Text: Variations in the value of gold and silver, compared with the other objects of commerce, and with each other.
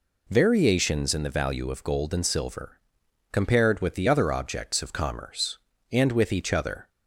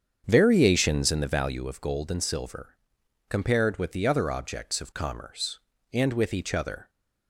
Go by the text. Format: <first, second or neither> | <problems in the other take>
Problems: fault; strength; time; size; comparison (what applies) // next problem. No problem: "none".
first | starts louder than the rest; strong; until 1.6 s; 7.5 dB